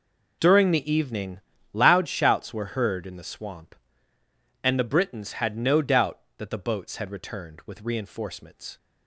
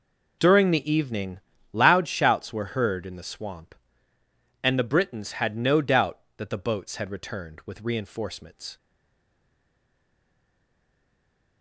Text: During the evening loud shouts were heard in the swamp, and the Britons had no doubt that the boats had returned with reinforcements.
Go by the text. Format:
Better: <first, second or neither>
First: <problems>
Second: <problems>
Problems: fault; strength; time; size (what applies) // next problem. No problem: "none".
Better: first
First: pauses between "evening" and "loud"; slight; at 1.3 s; 0.34 s long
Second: pauses between "evening" and "loud"; slight; at 1.3 s; 0.34 s long // stays silent after the last word; strong; from 8.7 s on; 2.9 s long